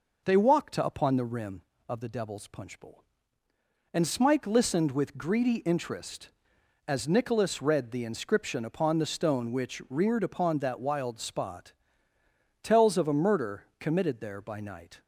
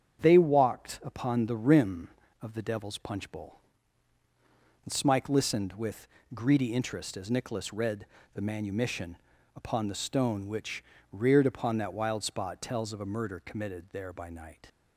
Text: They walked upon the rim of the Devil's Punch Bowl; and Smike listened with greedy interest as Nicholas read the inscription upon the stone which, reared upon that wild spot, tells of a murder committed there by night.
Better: first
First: none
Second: starts louder than the rest; strong; until 1.2 s; 8 dB // pauses between "with" and "greedy"; slight; at 6.0 s; 0.28 s long // pauses between "read" and "the"; slight; at 8.0 s; 0.30 s long // says "manumission" for "inscription"; at 8.4 s

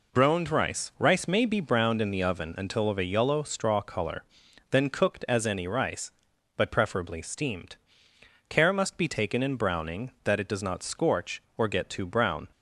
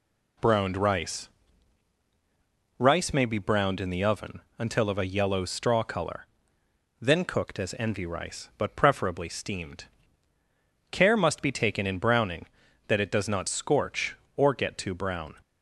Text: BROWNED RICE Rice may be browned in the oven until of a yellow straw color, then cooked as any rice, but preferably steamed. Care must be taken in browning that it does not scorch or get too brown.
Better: first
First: none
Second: pauses between "RICE" and "Rice"; strong; at 1.2 s; 1.4 s long // pauses between "oven" and "until"; slight; at 4.4 s; 0.18 s long // says "envy" for "any"; at 7.7 s

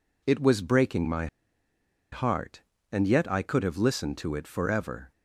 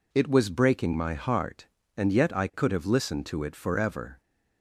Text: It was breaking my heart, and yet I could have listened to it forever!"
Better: second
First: pauses between "my" and "heart"; noticeable; at 1.2 s; 0.85 s long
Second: none

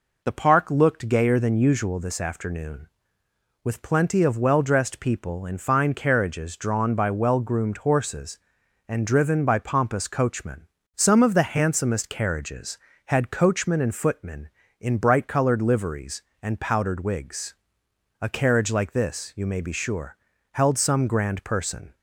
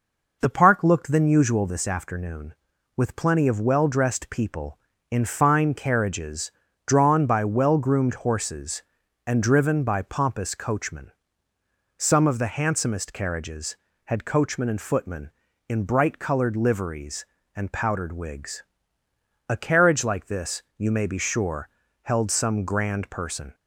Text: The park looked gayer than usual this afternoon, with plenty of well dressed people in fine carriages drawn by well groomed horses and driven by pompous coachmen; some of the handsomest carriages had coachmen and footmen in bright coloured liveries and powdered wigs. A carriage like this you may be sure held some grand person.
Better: first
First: pauses between "sure" and "held"; slight; at 20.1 s; 0.34 s long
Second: skips "gayer"; at 1.1 s // pauses between "carriages" and "drawn"; slight; at 6.5 s; 0.36 s long // pauses between "this" and "you"; slight; at 20.6 s; 0.16 s long // pauses between "sure" and "held"; slight; at 21.7 s; 0.32 s long

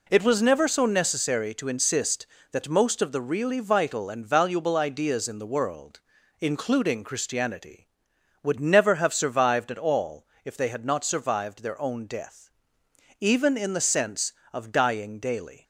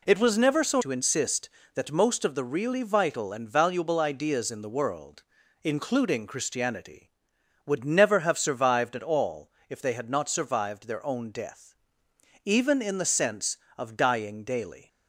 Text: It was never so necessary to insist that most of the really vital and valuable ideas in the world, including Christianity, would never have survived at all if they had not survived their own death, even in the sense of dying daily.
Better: first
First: pauses between "all" and "if"; slight; at 10.2 s; 0.16 s long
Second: skips "necessary"; at 0.8 s // pauses between "all" and "if"; slight; at 9.5 s; 0.16 s long

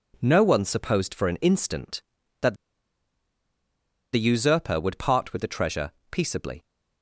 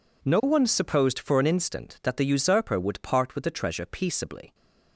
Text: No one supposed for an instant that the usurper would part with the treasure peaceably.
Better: second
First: pauses between "that" and "the"; strong; at 2.5 s; 1.5 s long // pauses between "treasure" and "peaceably"; slight; at 5.9 s; 0.18 s long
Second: none

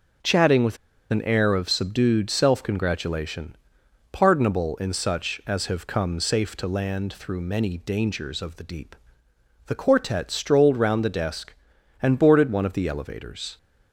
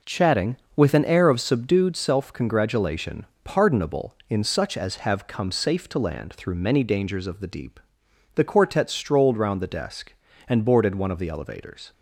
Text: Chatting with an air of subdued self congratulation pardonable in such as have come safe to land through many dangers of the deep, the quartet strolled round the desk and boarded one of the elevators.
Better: second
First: pauses between "with" and "an"; slight; at 0.7 s; 0.33 s long // pauses between "congratulation" and "pardonable"; noticeable; at 3.5 s; 0.56 s long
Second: pauses between "congratulation" and "pardonable"; slight; at 3.2 s; 0.20 s long

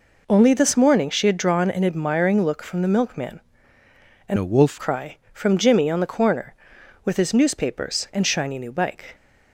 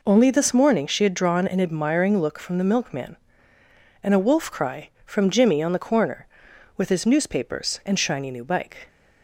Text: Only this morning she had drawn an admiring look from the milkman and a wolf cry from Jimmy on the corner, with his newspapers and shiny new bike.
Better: second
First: changes voice from "a" to "wolf"; from 4.3 to 4.8 s; 0.5 s long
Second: none

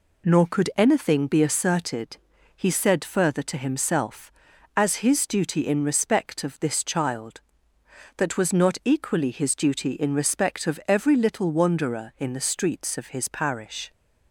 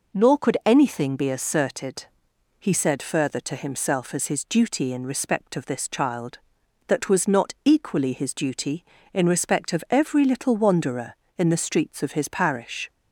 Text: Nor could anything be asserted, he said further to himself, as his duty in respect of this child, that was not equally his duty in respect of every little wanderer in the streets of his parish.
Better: neither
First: none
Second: none

